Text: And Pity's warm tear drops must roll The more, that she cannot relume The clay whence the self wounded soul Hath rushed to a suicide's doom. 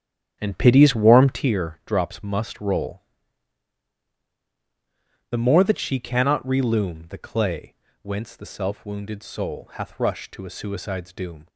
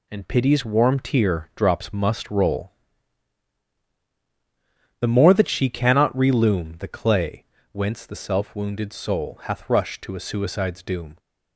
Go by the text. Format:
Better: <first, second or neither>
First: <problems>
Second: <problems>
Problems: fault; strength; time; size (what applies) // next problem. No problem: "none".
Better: second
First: starts louder than the rest; strong; until 1.5 s; 9.5 dB // pauses between "roll" and "The"; strong; at 3.0 s; 2.2 s long // pauses between "clay" and "whence"; slight; at 7.7 s; 0.28 s long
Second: pauses between "roll" and "The"; strong; at 2.7 s; 2.2 s long // pauses between "clay" and "whence"; slight; at 7.4 s; 0.28 s long